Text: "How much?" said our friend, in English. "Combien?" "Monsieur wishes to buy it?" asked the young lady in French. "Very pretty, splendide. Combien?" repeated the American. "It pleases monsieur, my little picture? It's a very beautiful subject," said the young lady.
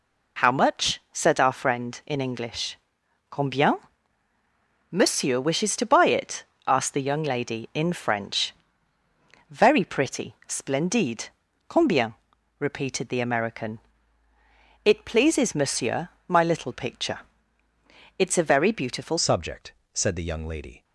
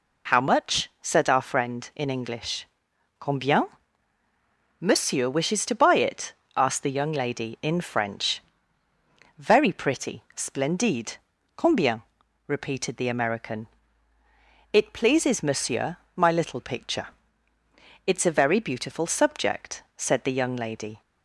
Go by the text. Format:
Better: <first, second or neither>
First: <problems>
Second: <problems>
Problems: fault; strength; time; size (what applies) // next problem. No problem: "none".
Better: second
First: changes voice at "subject"; from 19.1 s on; 1.7 s long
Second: none